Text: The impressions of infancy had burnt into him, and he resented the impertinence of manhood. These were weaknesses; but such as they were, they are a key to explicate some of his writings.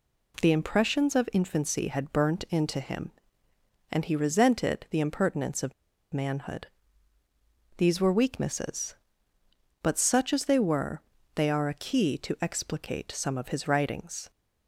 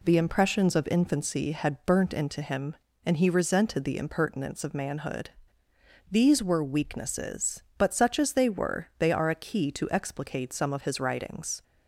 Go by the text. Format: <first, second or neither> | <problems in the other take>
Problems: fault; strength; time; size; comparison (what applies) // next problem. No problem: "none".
second | pauses between "of" and "manhood"; at 5.7 s; 0.41 s long